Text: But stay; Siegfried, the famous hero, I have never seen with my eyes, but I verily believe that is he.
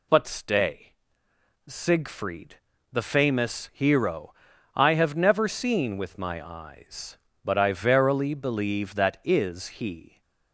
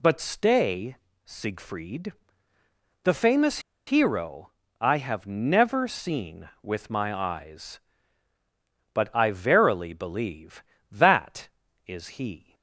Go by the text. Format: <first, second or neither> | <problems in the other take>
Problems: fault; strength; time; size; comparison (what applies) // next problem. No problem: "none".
first | pauses between "famous" and "hero"; slight; at 3.5 s; 0.27 s long